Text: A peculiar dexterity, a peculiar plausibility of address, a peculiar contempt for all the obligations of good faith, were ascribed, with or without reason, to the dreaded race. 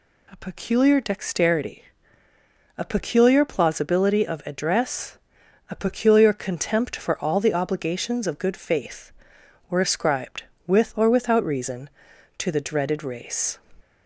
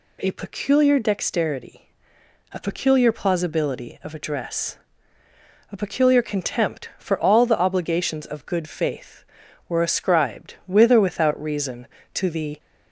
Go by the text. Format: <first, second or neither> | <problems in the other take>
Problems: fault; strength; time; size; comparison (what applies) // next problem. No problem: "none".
first | stops before "dreaded race"; at 12.5 s